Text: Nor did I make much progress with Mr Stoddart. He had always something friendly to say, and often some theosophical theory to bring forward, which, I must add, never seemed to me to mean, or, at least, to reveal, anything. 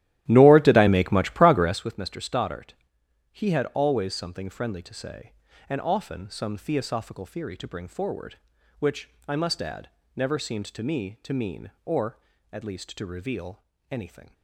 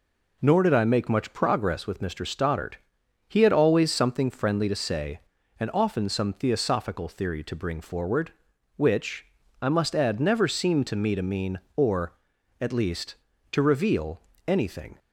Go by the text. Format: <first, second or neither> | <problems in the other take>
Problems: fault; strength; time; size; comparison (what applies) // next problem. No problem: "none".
second | starts louder than the rest; strong; until 1.9 s; 14 dB